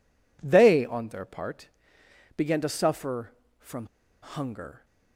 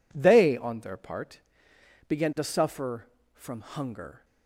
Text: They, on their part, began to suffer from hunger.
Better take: second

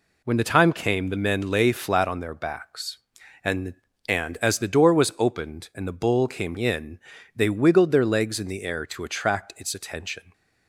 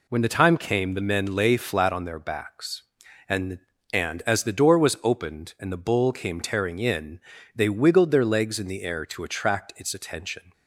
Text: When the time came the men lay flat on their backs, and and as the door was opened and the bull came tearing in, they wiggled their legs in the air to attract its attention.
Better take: second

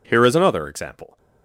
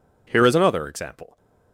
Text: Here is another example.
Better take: neither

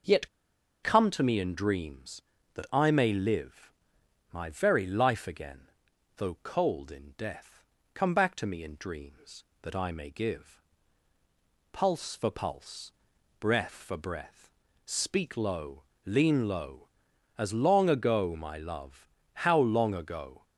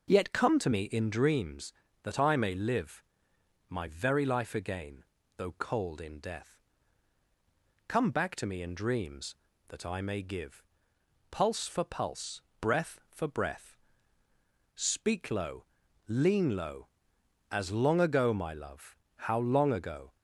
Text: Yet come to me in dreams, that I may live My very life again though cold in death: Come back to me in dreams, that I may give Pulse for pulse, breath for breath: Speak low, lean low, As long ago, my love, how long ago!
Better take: second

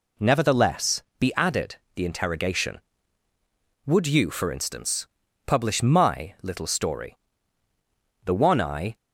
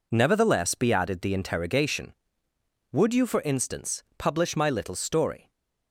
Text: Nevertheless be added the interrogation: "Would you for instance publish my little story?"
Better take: second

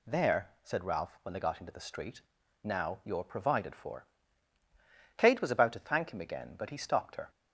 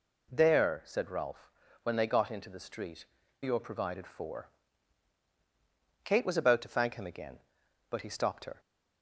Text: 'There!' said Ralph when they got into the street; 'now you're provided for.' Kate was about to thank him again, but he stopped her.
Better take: first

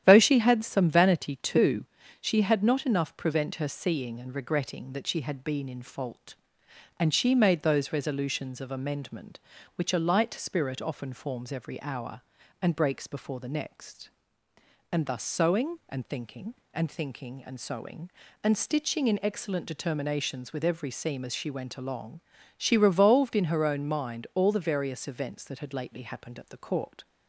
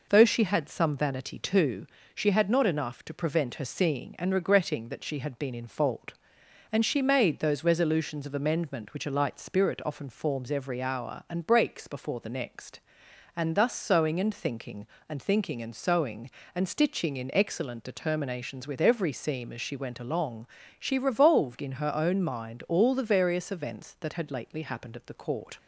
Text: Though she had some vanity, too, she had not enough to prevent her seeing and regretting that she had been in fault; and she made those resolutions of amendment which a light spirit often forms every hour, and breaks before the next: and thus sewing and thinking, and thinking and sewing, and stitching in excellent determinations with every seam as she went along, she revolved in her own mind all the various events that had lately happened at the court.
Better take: second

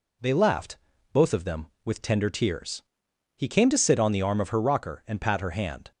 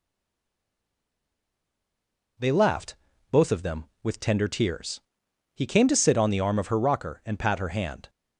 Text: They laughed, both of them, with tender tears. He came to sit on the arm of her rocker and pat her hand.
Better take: first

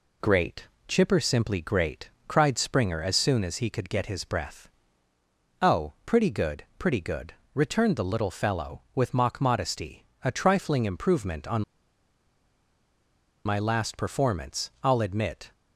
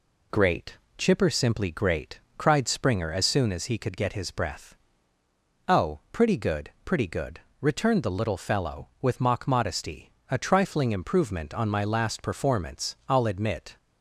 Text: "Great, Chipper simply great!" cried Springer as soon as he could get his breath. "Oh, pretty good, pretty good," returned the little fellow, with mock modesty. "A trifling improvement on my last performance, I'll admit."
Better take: second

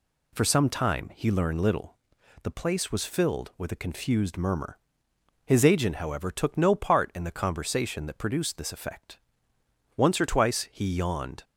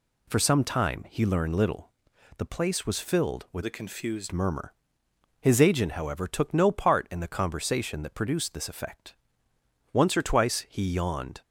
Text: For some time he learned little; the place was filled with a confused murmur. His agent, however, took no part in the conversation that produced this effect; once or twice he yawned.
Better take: first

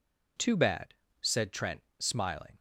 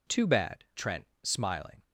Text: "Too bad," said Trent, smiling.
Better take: first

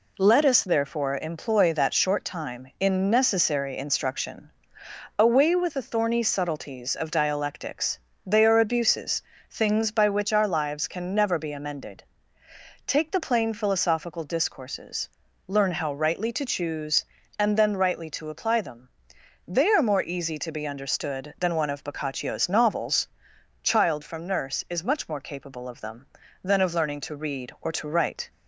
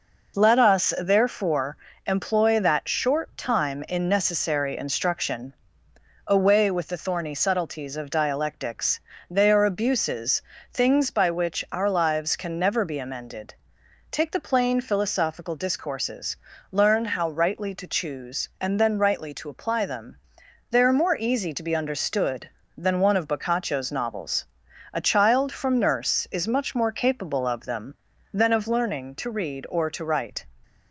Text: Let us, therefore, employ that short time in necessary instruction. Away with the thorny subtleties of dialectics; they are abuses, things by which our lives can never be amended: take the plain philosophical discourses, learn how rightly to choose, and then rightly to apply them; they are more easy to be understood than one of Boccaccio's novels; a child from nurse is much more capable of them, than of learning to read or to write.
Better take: second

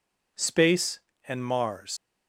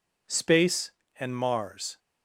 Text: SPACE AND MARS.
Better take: second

